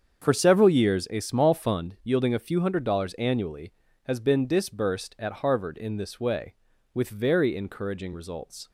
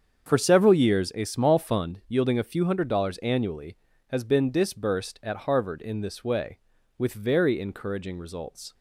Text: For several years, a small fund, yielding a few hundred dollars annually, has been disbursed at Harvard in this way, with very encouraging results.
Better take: neither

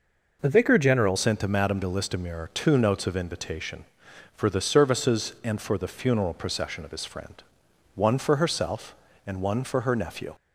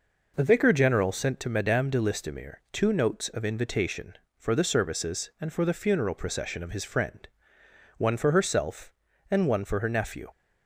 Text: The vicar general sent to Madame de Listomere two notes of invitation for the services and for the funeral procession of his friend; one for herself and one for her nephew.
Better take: second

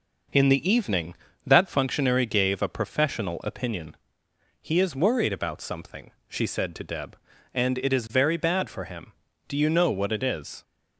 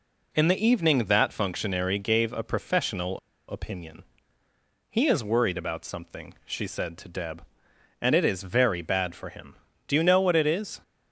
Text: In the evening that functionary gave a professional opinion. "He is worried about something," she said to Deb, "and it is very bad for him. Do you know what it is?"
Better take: first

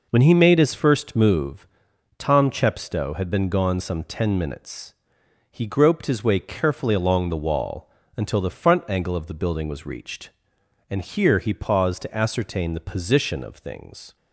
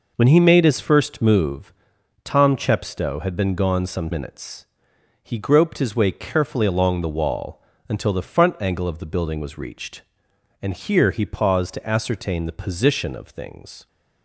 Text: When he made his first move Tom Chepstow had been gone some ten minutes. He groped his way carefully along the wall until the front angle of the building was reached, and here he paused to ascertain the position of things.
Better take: first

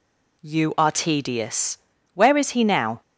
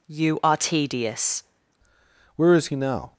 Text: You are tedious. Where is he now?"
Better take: first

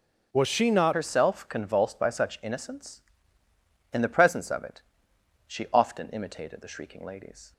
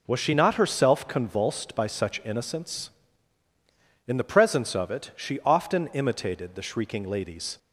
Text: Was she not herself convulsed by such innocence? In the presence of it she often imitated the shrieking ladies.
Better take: second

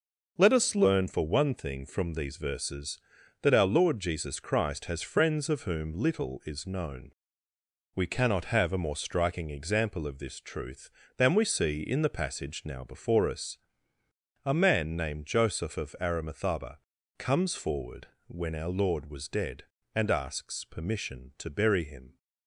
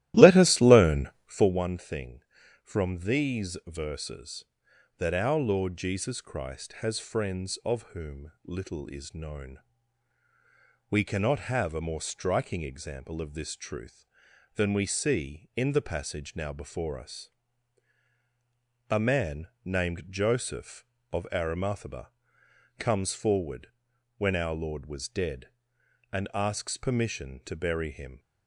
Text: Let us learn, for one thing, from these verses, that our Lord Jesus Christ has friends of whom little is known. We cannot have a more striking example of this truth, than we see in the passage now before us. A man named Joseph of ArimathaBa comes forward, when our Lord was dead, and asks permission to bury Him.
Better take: first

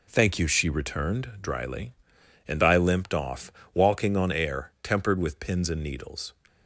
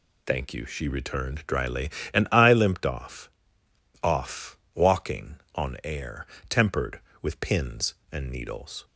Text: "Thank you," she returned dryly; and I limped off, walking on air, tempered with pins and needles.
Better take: first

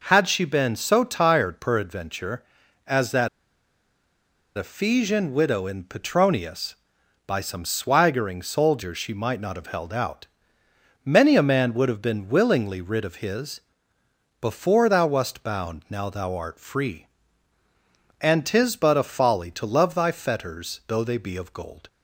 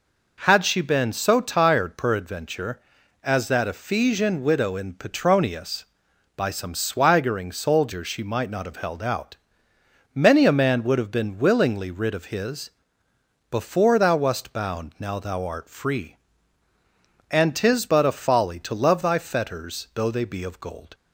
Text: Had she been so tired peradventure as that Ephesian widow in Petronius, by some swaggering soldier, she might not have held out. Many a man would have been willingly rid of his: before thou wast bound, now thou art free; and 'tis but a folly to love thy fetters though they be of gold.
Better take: second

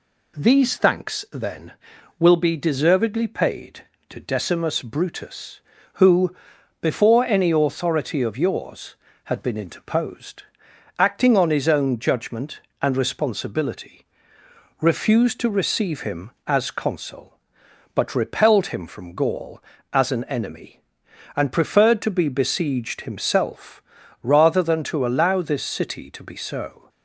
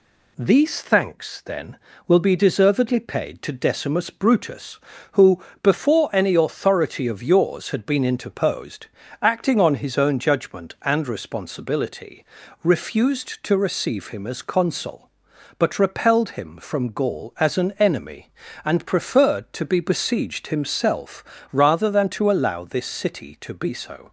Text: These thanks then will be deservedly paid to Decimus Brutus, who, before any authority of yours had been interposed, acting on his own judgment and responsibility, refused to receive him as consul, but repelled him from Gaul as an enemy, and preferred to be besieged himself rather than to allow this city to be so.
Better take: neither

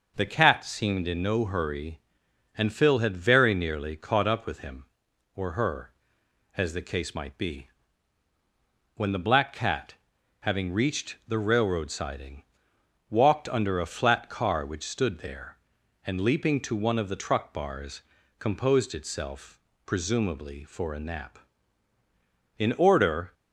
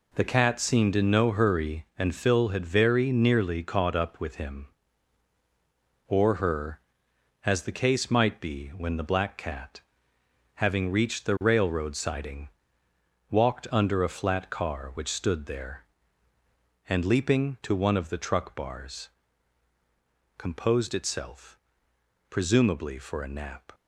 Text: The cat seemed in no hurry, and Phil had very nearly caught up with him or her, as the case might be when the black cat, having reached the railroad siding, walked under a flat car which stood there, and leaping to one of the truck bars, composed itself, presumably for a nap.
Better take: second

